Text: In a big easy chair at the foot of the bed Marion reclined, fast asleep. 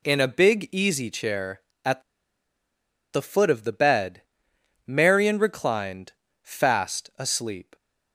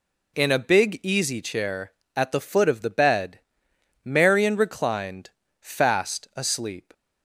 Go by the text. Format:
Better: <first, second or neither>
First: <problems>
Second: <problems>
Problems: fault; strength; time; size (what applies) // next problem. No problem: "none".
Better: second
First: pauses between "at" and "the"; at 2.0 s; 1.1 s long // pauses between "bed" and "Marion"; noticeable; at 4.2 s; 0.64 s long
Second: pauses between "bed" and "Marion"; noticeable; at 3.4 s; 0.64 s long